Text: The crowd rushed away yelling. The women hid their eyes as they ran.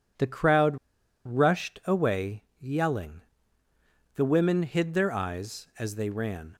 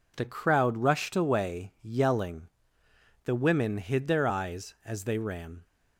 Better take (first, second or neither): second